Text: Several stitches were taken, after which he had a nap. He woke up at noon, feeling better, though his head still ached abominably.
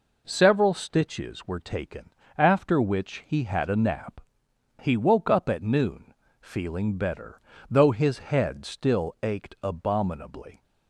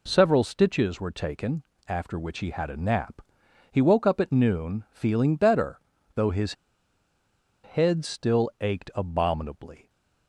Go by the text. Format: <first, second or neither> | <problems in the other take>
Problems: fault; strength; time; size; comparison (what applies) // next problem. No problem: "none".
first | pauses between "his" and "head"; at 6.5 s; 1.1 s long